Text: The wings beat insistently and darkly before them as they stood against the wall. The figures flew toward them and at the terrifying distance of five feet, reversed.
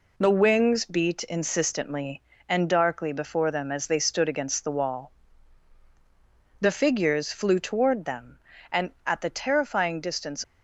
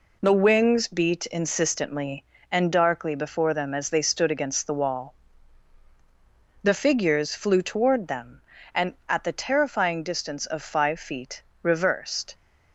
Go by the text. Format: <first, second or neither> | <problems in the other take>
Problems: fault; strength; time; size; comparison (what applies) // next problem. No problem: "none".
second | stops before "of five feet reversed"; at 10.4 s